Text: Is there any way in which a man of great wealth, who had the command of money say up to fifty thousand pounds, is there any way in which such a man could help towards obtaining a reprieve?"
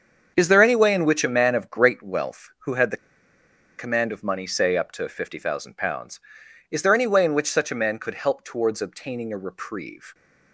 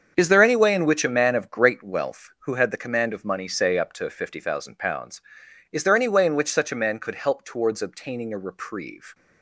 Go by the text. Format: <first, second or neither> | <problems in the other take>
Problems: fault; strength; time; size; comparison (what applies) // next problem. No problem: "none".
second | starts louder than the rest; until 1.3 s; 7 dB; strong in the second // pauses between "the" and "command"; noticeable; at 2.9 s; 0.80 s long